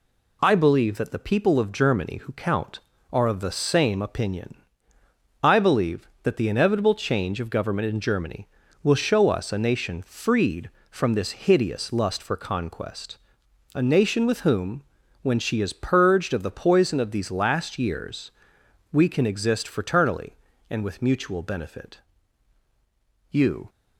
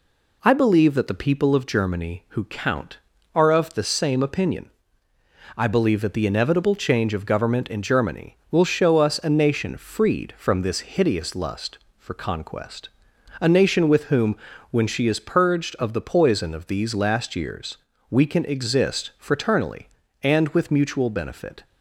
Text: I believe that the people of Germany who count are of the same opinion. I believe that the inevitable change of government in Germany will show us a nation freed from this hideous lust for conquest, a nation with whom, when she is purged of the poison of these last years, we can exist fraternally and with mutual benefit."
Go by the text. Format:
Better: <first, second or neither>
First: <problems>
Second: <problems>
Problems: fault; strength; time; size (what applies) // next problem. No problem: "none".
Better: second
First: goes on to say "You"; slight; from 23.2 s on; 0.40 s long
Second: none